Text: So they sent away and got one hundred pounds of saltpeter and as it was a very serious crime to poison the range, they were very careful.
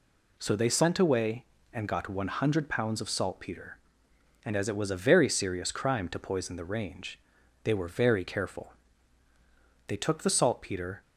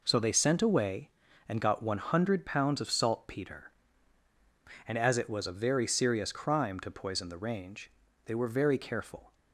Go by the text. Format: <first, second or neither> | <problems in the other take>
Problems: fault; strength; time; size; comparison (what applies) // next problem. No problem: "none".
second | goes on to say "They took the saltpeter"; noticeable; from 9.8 s on; 1.1 s long